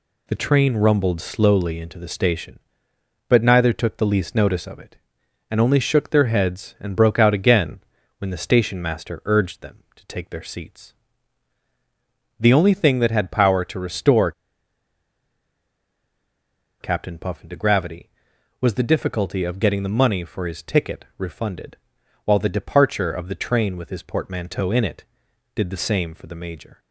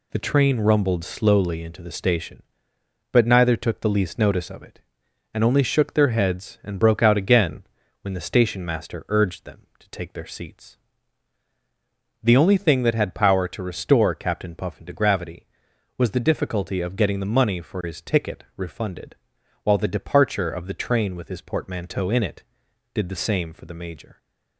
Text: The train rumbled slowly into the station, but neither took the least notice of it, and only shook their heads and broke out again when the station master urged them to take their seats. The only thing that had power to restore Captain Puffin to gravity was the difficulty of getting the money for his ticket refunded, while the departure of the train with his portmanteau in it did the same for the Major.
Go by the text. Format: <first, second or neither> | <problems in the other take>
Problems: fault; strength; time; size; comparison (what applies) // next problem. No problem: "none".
second | pauses between "again" and "when"; at 7.7 s; 0.40 s long; also in the second // pauses between "restore" and "Captain"; strong; at 14.3 s; 2.4 s long